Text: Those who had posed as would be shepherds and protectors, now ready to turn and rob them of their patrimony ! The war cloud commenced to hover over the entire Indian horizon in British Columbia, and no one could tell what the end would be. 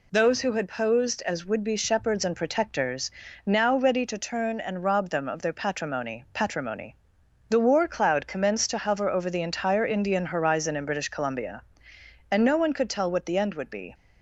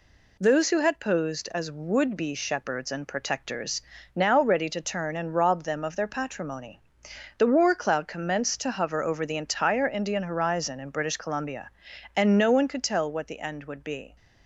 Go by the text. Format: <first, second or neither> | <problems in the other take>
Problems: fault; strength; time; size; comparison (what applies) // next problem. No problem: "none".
second | says "patrimony" twice; at 6.3 s